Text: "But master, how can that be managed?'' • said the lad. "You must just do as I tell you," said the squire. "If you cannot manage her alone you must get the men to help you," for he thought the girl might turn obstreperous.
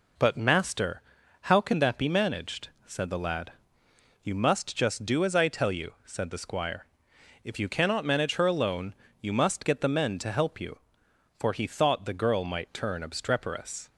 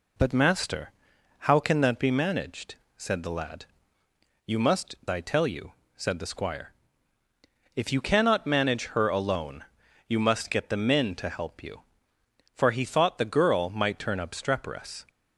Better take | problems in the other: first | skips "just do as"; at 5.0 s // pauses between "alone" and "you"; at 9.6 s; 0.42 s long; slight in the first

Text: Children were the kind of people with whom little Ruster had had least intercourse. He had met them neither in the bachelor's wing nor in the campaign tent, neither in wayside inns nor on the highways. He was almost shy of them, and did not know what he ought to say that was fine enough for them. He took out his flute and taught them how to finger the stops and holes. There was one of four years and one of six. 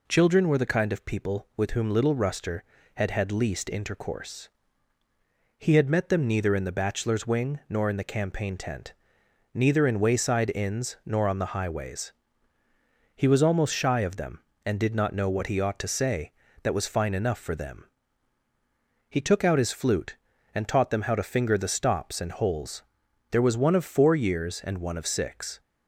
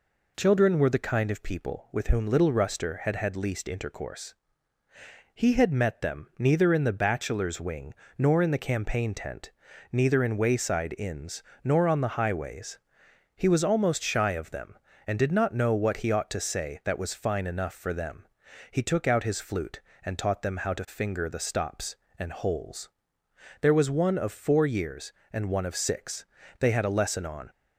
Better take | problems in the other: first | pauses between "wing" and "nor"; slight; at 7.9 s; 0.24 s long // pauses between "inns" and "nor"; slight; at 11.4 s; 0.22 s long // goes on to say "They had a lesson on"; noticeable; from 26.5 s on; 0.90 s long

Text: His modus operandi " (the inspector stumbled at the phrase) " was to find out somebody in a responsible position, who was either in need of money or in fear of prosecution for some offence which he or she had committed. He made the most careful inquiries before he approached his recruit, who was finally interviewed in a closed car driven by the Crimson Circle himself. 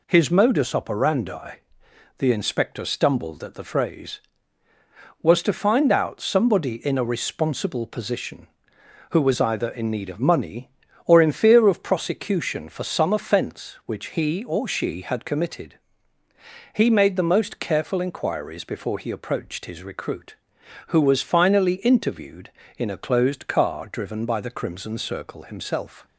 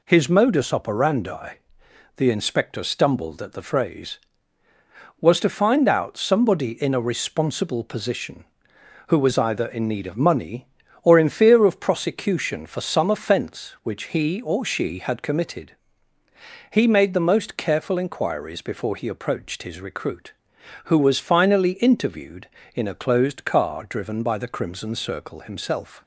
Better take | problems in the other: neither | none

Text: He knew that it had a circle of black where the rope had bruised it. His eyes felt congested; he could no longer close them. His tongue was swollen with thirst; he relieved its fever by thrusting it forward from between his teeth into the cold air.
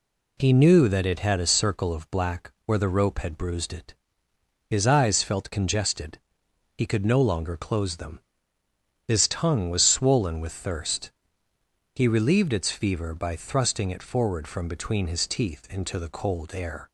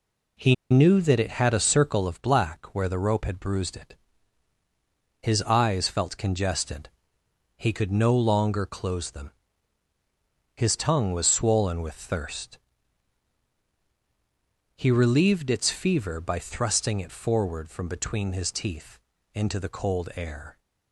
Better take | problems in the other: first | pauses between "He" and "knew"; slight; at 0.5 s; 0.15 s long // pauses between "teeth" and "into"; slight; at 18.9 s; 0.34 s long

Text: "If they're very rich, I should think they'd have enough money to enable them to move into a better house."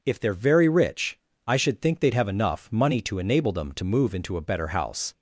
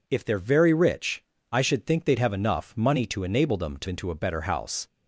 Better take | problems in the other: first | skips "move"; at 3.8 s

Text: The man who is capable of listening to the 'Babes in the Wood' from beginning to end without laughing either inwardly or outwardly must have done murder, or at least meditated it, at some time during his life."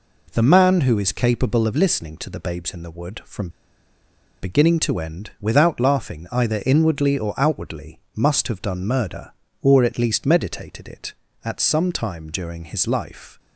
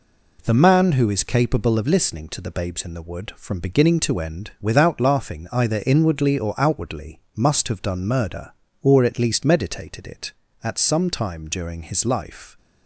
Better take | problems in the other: second | pauses between "from" and "beginning"; noticeable; at 3.4 s; 0.93 s long // pauses between "outwardly" and "must"; slight; at 7.9 s; 0.16 s long; slight in the second

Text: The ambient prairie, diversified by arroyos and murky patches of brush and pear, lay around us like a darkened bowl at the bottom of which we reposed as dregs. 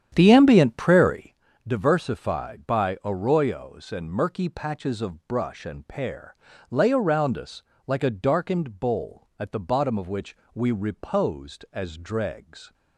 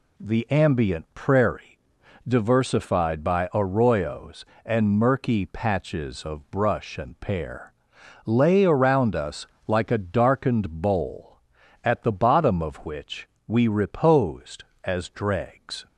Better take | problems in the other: second | starts louder than the rest; strong; until 1.5 s; 9.5 dB // pauses between "us" and "like"; slight; at 7.6 s; 0.24 s long; slight in the second // pauses between "which" and "we"; slight; at 10.3 s; 0.18 s long; slight in the second

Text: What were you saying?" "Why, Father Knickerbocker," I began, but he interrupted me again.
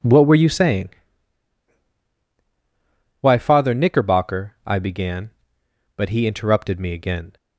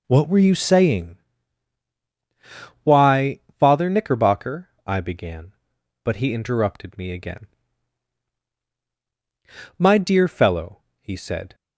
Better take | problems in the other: first | goes on to say "My dear fellow he said"; strong; from 9.7 s on; 1.7 s long

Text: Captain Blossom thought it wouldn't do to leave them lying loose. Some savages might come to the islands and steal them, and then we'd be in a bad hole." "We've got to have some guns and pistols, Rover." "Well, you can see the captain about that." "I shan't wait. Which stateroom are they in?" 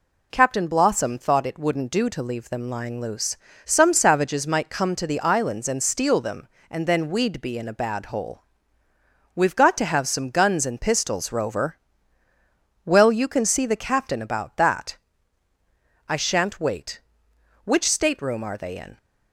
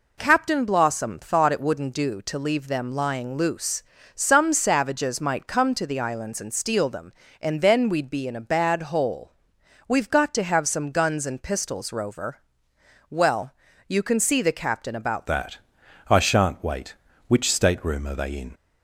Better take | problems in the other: first | changes voice at "that"; from 15.2 s on; 3.3 s long

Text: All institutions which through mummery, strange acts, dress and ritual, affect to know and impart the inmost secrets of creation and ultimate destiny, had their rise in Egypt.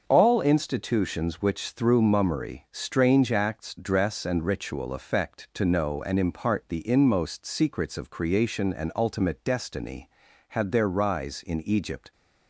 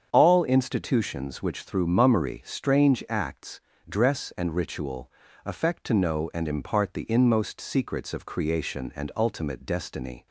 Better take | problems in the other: first | starts louder than the rest; strong; until 1.1 s; 7.5 dB; also in the first // stops before "had their rise in Egypt"; at 10.2 s

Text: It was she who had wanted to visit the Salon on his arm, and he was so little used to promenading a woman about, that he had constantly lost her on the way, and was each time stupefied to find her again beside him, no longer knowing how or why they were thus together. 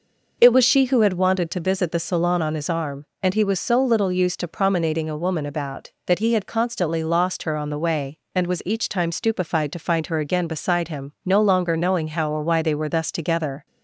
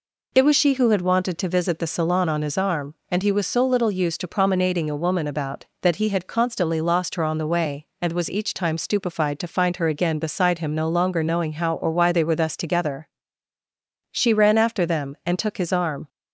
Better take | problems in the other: first | goes on to say "She ran after them and took his arm"; strong; from 14.1 s on; 1.9 s long

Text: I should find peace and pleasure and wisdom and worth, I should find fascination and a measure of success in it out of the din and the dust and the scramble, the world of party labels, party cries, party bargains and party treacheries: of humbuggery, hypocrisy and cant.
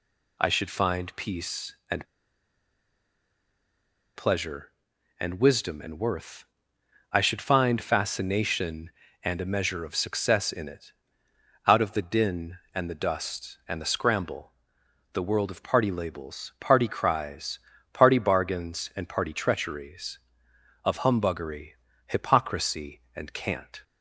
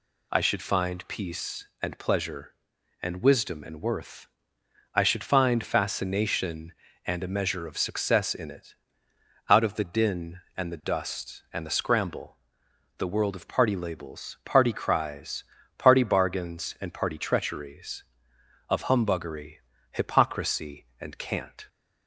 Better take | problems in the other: second | pauses between "and" and "pleasure"; strong; at 2.0 s; 2.0 s long // pauses between "it" and "out"; noticeable; at 10.9 s; 0.74 s long; noticeable in the second

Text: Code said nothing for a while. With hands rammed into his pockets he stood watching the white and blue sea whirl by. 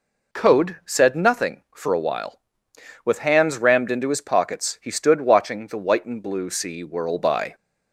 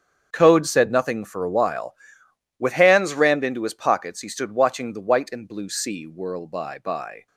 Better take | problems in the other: first | starts louder than the rest; strong; until 1.3 s; 7.5 dB // says "by" twice; at 6.7 s

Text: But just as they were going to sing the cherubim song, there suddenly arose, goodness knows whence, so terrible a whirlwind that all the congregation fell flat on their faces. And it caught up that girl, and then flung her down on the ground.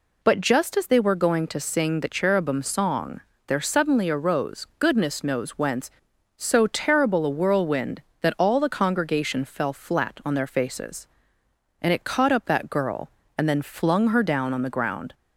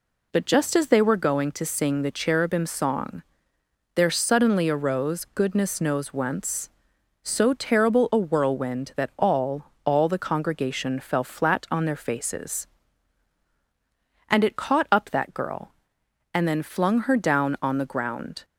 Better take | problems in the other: first | says "all" twice; at 9.8 s

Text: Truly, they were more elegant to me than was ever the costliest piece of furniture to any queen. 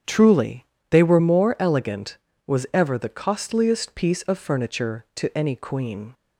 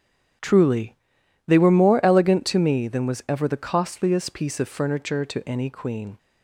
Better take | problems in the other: second | starts louder than the rest; strong; until 1.3 s; 8.5 dB; strong in the second // skips "to me than"; at 2.3 s

